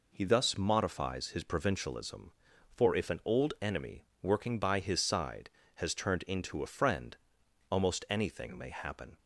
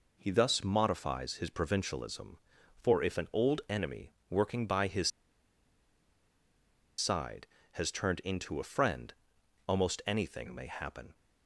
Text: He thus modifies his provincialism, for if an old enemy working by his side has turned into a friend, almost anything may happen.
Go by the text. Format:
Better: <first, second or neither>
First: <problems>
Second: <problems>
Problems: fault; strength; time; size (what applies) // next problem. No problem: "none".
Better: first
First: pauses between "enemy" and "working"; slight; at 4.0 s; 0.18 s long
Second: pauses between "enemy" and "working"; slight; at 4.1 s; 0.18 s long // pauses between "his" and "side"; strong; at 5.0 s; 1.8 s long